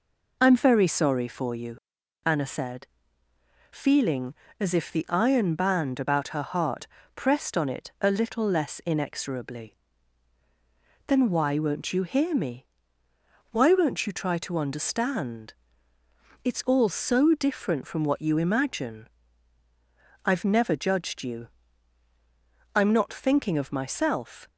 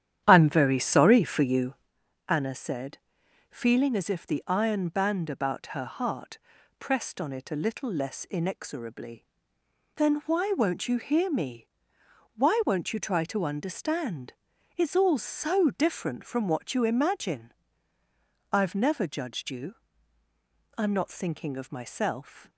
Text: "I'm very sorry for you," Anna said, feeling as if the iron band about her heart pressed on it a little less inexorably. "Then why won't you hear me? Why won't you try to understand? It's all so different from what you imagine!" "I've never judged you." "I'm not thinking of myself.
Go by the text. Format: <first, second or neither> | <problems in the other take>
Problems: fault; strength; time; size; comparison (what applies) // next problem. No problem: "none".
first | starts louder than the rest; strong; until 1.9 s; 10.5 dB // pauses between "heart" and "pressed"; at 6.3 s; 0.42 s long; slight in the first